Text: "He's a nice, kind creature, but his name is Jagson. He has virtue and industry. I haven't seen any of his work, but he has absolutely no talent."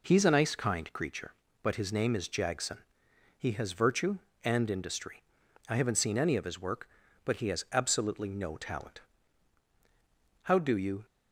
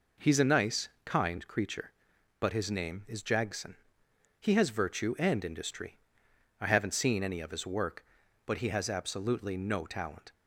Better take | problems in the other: second | goes on to say "How do you"; noticeable; from 10.4 s on; 0.62 s long

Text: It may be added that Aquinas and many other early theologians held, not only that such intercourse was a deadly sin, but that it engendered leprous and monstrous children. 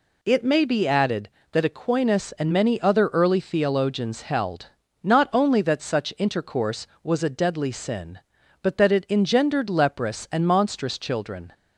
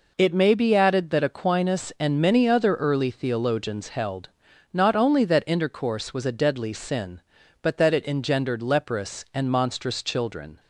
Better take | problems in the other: first | skips "such"; at 5.4 s

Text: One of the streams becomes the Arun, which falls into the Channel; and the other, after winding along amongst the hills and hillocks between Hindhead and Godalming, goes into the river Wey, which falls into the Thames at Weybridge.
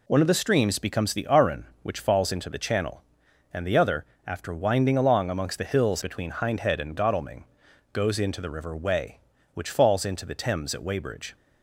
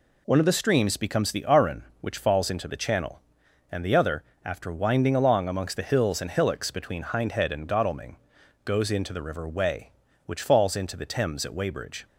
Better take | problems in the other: second | skips "and hillocks"; at 6.0 s

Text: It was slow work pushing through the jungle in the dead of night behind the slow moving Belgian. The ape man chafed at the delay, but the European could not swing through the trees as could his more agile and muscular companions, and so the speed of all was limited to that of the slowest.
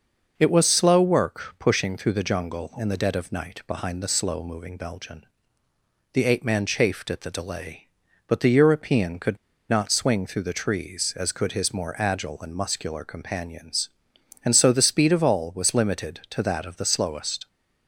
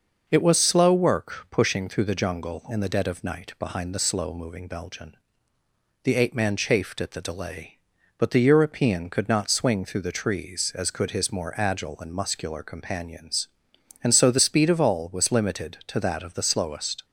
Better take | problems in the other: second | pauses between "could" and "not"; slight; at 9.3 s; 0.32 s long

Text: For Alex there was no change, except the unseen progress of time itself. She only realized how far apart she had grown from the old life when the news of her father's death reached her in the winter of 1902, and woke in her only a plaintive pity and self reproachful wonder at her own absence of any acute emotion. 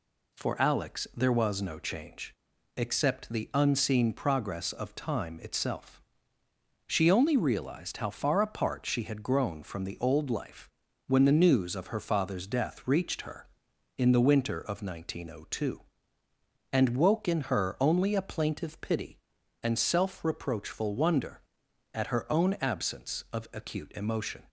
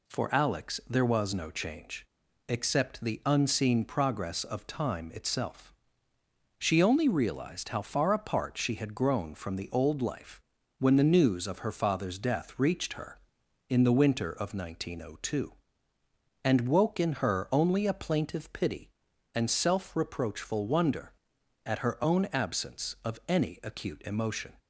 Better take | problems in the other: second | pauses between "life" and "when"; at 10.6 s; 0.38 s long; also in the second // skips "any"; at 23.5 s

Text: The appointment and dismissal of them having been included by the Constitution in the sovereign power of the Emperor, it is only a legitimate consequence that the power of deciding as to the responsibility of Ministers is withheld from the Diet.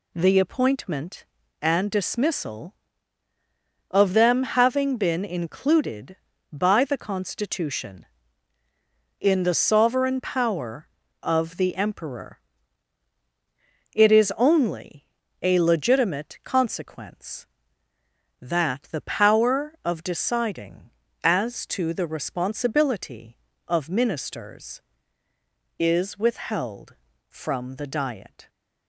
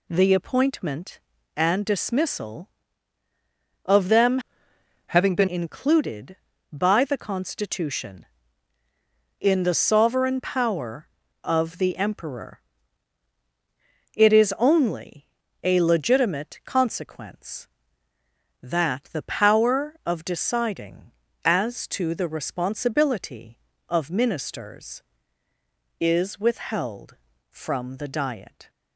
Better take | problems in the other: first | changes voice from "having" to "been"; from 5.0 to 5.4 s; 0.4 s long // pauses between "only" and "a"; slight; at 15.2 s; 0.34 s long; slight in the first

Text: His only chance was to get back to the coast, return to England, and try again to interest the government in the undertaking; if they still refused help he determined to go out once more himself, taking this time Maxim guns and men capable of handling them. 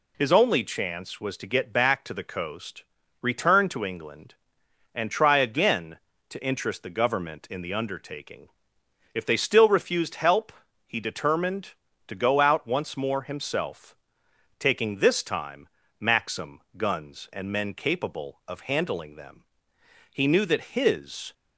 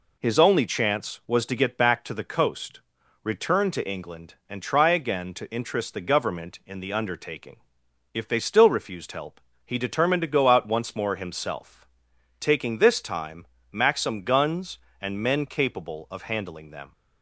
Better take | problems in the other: second | pauses between "help" and "he"; slight; at 10.5 s; 0.34 s long; slight in the second // pauses between "time" and "Maxim"; slight; at 15.6 s; 0.32 s long; slight in the second // pauses between "Maxim" and "guns"; slight; at 16.6 s; 0.16 s long // goes on to say "He knew that his"; noticeable; from 20.1 s on; 1.2 s long

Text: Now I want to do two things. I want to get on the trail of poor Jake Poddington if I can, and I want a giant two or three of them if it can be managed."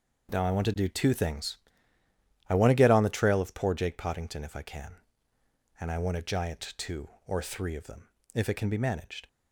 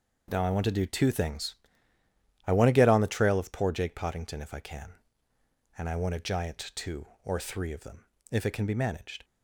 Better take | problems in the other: neither | pauses between "them" and "if"; slight; the same in both

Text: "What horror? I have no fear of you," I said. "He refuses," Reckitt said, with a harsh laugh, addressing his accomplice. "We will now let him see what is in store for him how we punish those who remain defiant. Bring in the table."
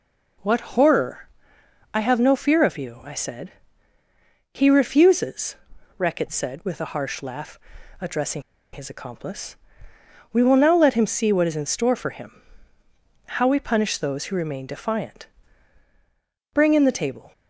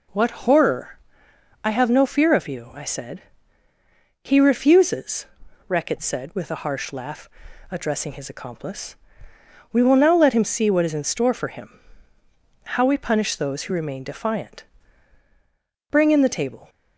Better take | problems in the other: second | pauses between "addressing" and "his"; slight; at 8.4 s; 0.31 s long // pauses between "him" and "how"; noticeable; at 12.4 s; 0.84 s long; noticeable in the second

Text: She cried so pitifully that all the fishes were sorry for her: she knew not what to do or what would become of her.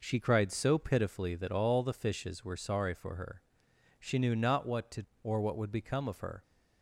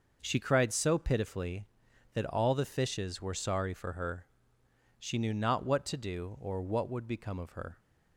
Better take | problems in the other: second | skips "do"; at 5.1 s

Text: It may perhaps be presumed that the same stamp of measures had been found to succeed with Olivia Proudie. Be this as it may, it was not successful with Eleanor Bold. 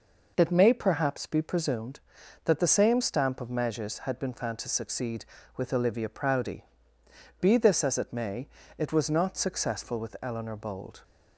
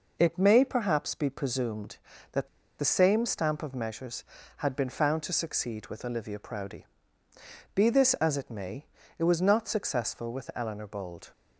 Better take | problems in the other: first | pauses between "that" and "the"; slight; at 2.4 s; 0.32 s long

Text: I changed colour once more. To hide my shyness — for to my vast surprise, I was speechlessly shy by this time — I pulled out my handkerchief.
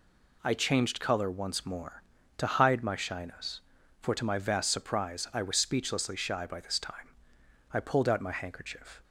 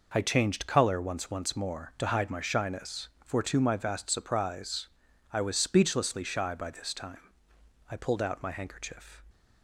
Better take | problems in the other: first | says "once" twice; at 1.3 s

